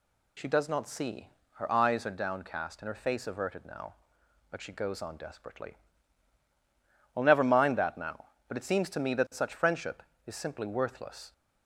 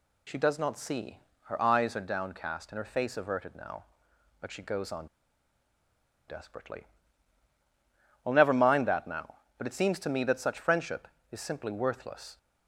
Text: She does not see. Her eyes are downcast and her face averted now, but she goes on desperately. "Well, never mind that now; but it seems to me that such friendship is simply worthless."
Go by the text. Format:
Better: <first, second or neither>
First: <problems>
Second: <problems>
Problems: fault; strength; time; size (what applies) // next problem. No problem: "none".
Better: first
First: none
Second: pauses between "on" and "desperately"; at 5.0 s; 1.2 s long